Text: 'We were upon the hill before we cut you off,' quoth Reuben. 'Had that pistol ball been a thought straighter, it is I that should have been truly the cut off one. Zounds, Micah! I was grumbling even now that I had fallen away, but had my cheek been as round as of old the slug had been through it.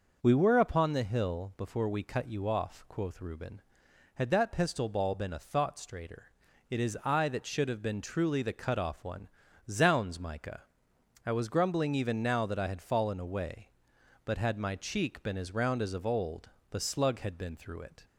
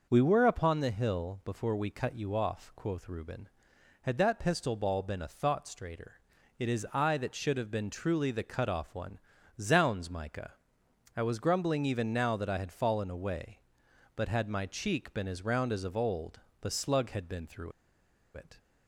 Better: first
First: pauses between "old" and "the"; slight; at 16.4 s; 0.20 s long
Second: pauses between "old" and "the"; slight; at 16.3 s; 0.20 s long // pauses between "through" and "it"; noticeable; at 17.7 s; 0.63 s long

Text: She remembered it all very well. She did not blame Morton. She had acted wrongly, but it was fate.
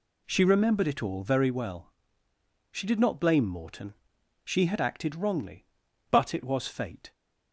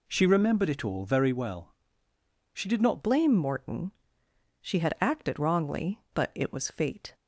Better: first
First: none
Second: changes voice at "blame"; from 3.0 s on; 4.1 s long

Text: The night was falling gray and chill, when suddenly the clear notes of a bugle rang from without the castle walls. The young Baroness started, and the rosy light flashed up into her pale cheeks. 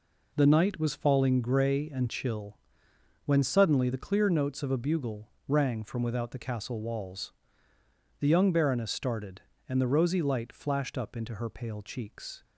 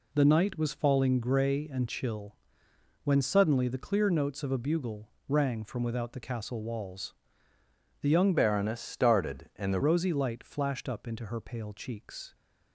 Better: first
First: pauses between "bugle" and "rang"; slight; at 5.2 s; 0.20 s long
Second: pauses between "bugle" and "rang"; slight; at 5.0 s; 0.20 s long // changes voice from "Baroness" to "the"; from 8.3 to 9.7 s; 1.4 s long

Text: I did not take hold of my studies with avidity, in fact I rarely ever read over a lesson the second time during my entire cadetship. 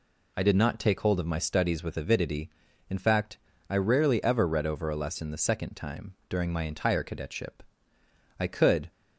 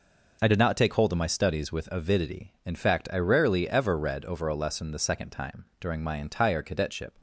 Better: second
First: pauses between "fact" and "I"; slight; at 3.3 s; 0.32 s long // pauses between "time" and "during"; slight; at 6.1 s; 0.16 s long // goes on to say "I could"; from 8.3 s on; 0.52 s long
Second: pauses between "time" and "during"; slight; at 5.6 s; 0.16 s long

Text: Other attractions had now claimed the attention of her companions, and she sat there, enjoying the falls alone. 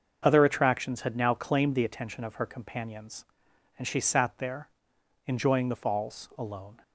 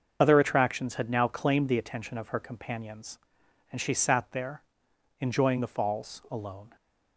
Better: first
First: starts louder than the rest; noticeable; until 1.2 s; 6 dB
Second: loses the start of "Other"; at 0.2 s; 25 ms // starts louder than the rest; noticeable; until 1.2 s; 6 dB

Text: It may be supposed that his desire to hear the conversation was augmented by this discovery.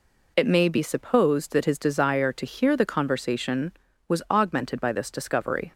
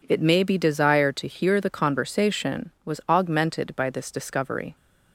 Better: first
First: none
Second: skips "supposed that his"; at 0.5 s

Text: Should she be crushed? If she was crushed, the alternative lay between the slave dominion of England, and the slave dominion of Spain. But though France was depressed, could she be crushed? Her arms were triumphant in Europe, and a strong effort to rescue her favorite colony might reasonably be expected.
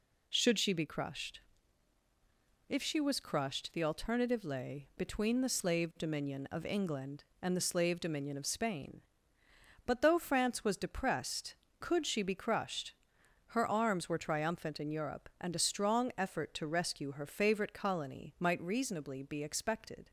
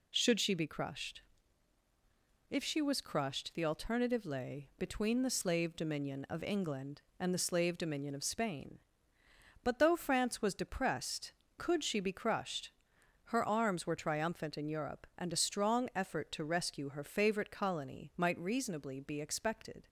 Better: neither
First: none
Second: none

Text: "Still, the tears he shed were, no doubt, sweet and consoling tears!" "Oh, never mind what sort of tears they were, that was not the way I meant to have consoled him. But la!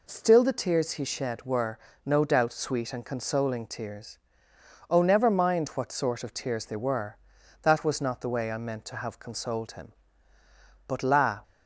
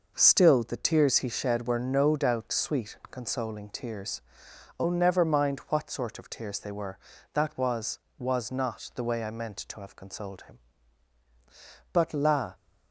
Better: first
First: none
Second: says "was" twice; at 8.1 s

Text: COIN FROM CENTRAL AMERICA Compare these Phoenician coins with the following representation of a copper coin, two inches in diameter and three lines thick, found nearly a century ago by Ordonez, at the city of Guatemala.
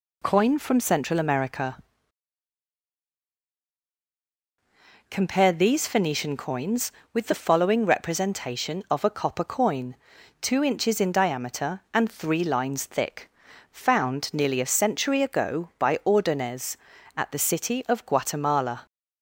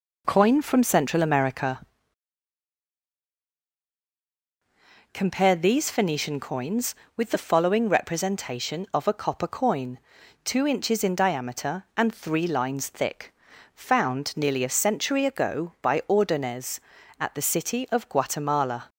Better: first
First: pauses between "AMERICA" and "Compare"; strong; at 1.7 s; 3.3 s long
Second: starts louder than the rest; noticeable; until 2.0 s; 4 dB // pauses between "AMERICA" and "Compare"; strong; at 1.8 s; 3.3 s long

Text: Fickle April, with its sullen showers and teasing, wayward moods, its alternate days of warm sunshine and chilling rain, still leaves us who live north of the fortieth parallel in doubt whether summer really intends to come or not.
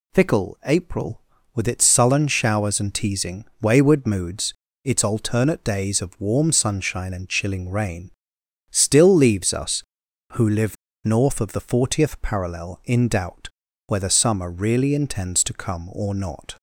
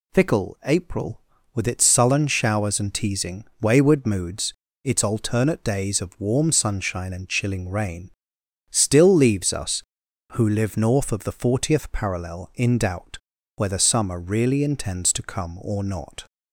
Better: second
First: pauses between "live" and "north"; slight; at 10.7 s; 0.28 s long // pauses between "doubt" and "whether"; at 13.4 s; 0.38 s long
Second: pauses between "doubt" and "whether"; at 13.1 s; 0.38 s long

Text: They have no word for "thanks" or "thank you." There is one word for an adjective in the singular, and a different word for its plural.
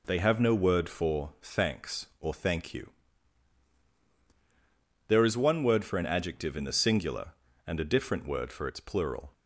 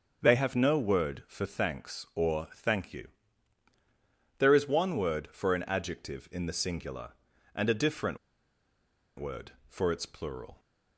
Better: first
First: none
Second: starts louder than the rest; until 1.2 s; 6 dB // pauses between "different" and "word"; at 8.1 s; 1.0 s long

